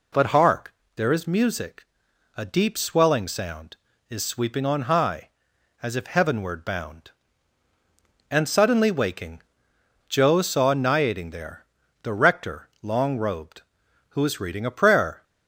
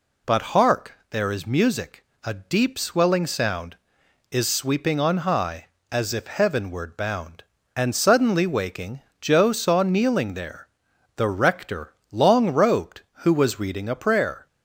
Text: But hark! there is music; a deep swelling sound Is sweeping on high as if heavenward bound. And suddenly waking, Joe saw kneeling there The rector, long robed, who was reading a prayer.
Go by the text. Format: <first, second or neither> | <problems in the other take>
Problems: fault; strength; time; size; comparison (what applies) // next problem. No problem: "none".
second | says "niating" for "kneeling"; at 10.7 s // pauses between "there" and "The"; at 11.6 s; 0.38 s long; noticeable in the second